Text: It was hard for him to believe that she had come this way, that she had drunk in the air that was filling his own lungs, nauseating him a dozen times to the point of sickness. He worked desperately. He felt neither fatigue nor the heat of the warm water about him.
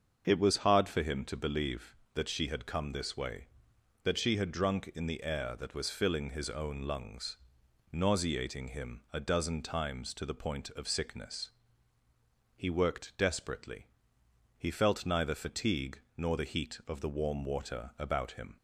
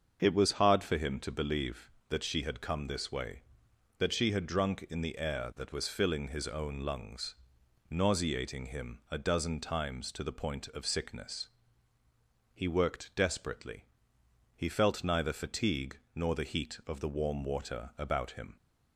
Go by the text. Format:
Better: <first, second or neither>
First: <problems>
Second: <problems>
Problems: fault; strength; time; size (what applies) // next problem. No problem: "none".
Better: neither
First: starts louder than the rest; until 1.2 s; 6.5 dB // pauses between "fatigue" and "nor"; slight; at 15.9 s; 0.18 s long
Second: starts louder than the rest; until 1.2 s; 6.5 dB // pauses between "fatigue" and "nor"; slight; at 15.9 s; 0.18 s long